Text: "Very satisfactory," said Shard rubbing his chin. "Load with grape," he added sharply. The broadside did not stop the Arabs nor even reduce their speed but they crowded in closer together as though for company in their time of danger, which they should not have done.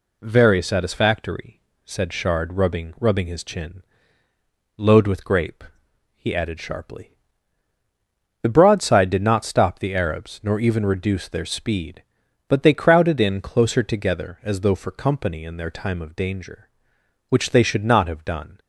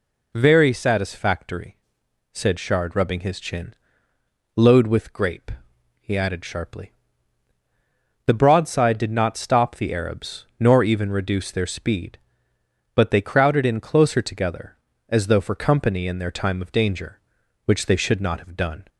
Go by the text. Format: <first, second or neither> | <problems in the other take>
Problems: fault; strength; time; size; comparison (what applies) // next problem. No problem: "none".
second | says "rubbing" twice; at 2.9 s